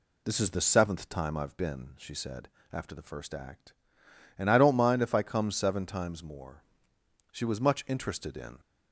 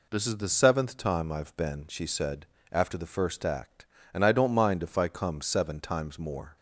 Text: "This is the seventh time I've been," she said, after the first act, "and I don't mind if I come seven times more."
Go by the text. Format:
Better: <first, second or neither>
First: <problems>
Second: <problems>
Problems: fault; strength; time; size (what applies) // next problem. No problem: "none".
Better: second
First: goes on to say "She was much interested in"; noticeable; from 7.2 s on; 1.3 s long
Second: none